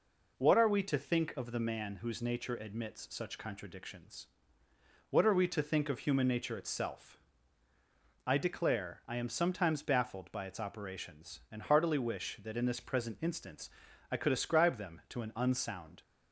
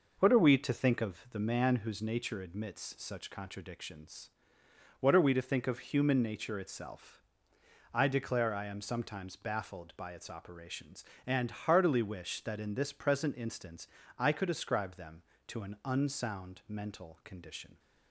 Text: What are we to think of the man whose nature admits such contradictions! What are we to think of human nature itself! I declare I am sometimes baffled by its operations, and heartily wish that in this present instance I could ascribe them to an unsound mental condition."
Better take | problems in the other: second | pauses between "instance" and "I"; at 13.6 s; 0.42 s long; slight in the second // stops before "mental condition"; at 16.0 s

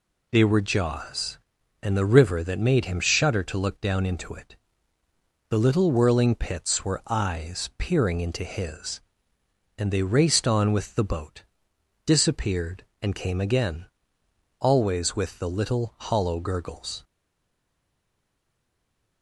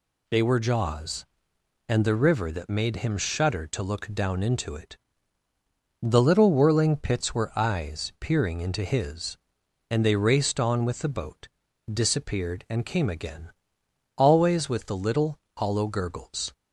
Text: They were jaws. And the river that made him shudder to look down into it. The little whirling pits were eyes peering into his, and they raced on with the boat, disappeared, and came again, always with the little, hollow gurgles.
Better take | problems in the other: second | stays silent after the last word; from 17.0 s on; 2.2 s long

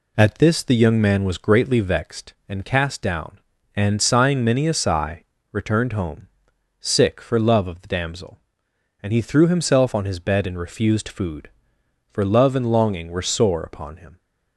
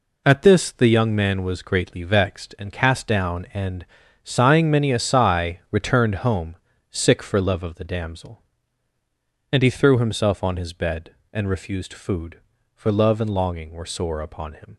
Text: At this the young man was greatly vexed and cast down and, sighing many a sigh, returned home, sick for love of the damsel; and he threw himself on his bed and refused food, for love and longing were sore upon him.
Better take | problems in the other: neither | none

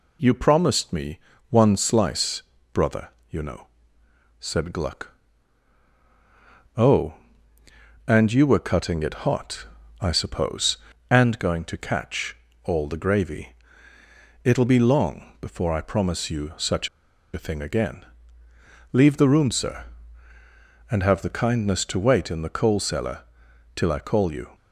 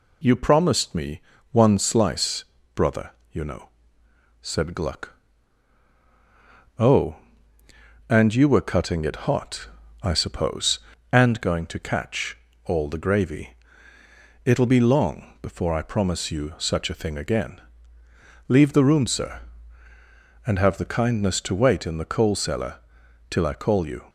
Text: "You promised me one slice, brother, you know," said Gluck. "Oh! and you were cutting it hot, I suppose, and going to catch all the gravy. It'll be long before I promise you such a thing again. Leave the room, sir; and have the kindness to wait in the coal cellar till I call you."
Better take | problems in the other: second | pauses between "me" and "one"; slight; at 1.1 s; 0.30 s long; slight in the second // pauses between "catch" and "all"; slight; at 12.3 s; 0.28 s long; slight in the second // pauses between "such" and "a"; noticeable; at 16.8 s; 0.47 s long // pauses between "cellar" and "till"; noticeable; at 23.1 s; 0.56 s long; noticeable in the second

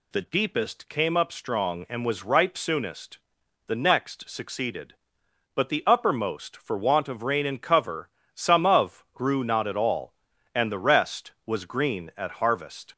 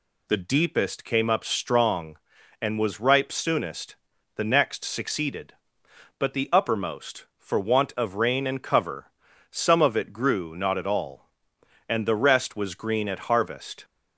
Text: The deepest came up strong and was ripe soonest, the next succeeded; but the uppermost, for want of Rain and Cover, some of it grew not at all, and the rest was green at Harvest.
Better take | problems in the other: second | skips "it"; at 9.1 s

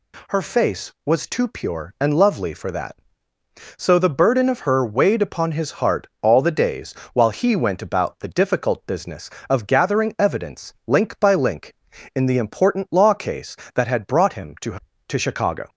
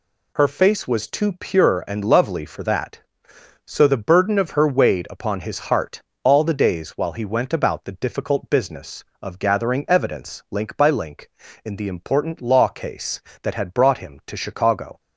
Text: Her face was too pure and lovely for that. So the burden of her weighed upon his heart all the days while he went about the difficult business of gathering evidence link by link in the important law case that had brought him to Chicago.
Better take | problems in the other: second | pauses between "heart" and "all"; slight; at 6.0 s; 0.16 s long; slight in the second // pauses between "days" and "while"; slight; at 6.9 s; 0.22 s long // says "to" twice; at 15.0 s

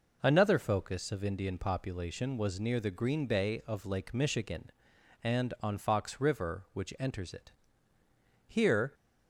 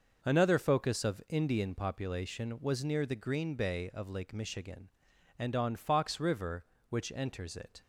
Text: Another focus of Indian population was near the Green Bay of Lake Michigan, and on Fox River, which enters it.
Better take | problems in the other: second | goes on to say "Here"; slight; from 8.4 s on; 0.46 s long

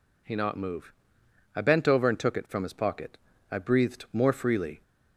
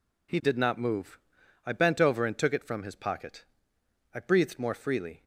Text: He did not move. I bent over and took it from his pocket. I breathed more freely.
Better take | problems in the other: second | skips "did"; at 0.3 s

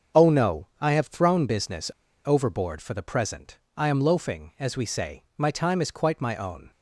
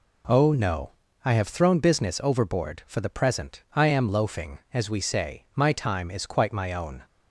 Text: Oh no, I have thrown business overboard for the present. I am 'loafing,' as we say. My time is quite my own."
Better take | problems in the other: second | starts louder than the rest; until 1.2 s; 7 dB // pauses between "business" and "overboard"; slight; at 1.9 s; 0.33 s long

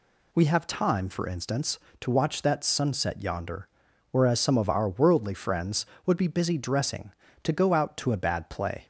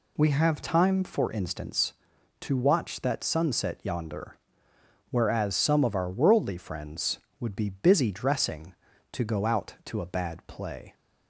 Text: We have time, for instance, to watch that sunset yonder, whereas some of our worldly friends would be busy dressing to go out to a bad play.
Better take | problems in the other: neither | none

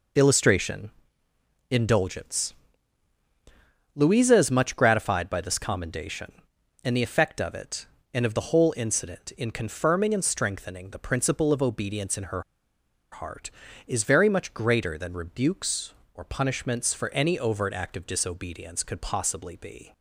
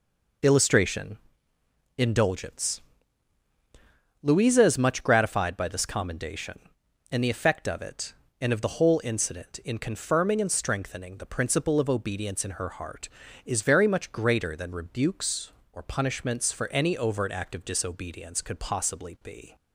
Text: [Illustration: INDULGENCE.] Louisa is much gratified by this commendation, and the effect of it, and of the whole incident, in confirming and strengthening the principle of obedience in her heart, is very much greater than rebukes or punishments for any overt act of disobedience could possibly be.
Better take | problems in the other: second | pauses between "her" and "heart"; noticeable; at 12.4 s; 0.70 s long

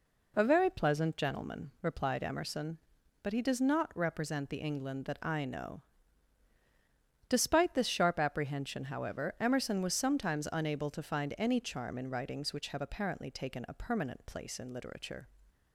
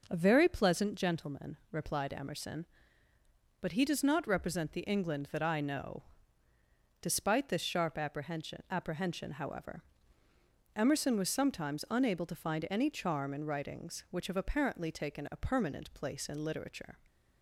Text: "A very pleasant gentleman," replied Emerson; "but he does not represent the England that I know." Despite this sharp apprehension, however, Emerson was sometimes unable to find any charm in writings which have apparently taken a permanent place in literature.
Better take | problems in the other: first | says "apprehension" twice; at 8.7 s

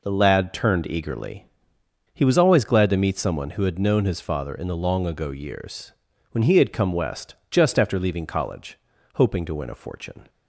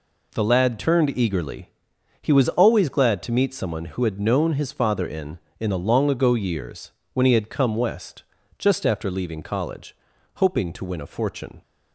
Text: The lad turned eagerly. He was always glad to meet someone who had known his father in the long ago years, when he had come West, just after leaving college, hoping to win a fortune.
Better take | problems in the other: first | says "in" twice; at 5.5 s

